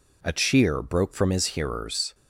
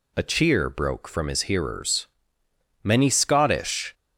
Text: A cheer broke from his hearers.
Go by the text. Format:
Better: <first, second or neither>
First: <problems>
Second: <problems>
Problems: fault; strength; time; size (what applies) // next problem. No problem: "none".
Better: first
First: none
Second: goes on to say "Many Scottish"; noticeable; from 2.8 s on; 1.1 s long